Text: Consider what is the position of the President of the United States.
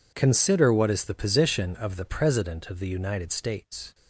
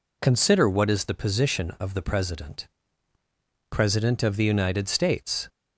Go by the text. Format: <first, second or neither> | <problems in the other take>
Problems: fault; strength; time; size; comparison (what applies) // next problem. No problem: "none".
first | says "President" twice; at 3.7 s